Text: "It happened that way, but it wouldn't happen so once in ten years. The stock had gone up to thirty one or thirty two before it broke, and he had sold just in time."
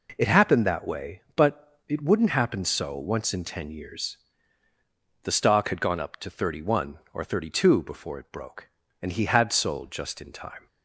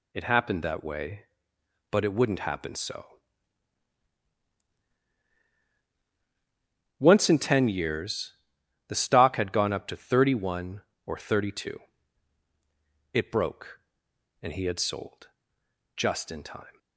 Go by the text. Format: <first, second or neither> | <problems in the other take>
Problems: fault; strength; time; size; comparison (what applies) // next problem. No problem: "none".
first | pauses between "so" and "once"; strong; at 3.0 s; 3.9 s long // skips "before"; at 12.4 s // pauses between "sold" and "just"; noticeable; at 15.2 s; 0.68 s long